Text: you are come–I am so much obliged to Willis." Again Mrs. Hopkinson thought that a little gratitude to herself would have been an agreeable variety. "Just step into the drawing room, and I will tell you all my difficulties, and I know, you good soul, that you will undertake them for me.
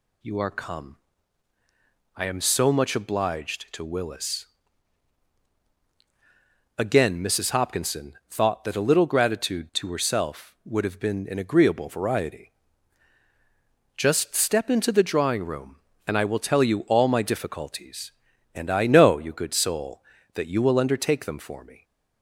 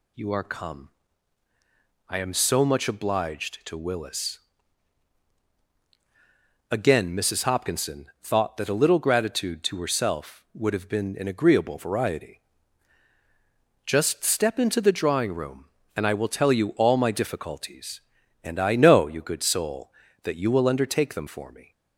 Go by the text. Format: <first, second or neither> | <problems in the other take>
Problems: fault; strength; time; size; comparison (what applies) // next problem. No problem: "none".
neither | pauses between "Hopkinson" and "thought"; slight; the same in both